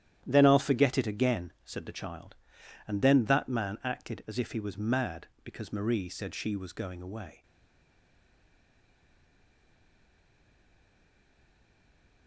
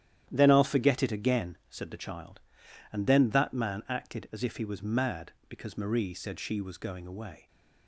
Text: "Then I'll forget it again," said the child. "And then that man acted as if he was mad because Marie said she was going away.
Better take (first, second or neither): second